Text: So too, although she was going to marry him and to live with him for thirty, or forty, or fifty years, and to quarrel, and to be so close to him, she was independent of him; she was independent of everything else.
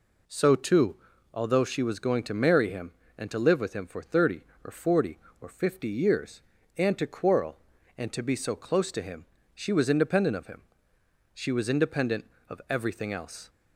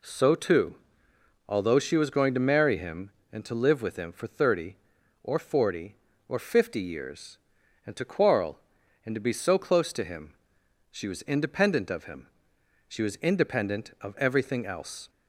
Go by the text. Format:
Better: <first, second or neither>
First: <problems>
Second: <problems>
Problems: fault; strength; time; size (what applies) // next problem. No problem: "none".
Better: neither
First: none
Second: none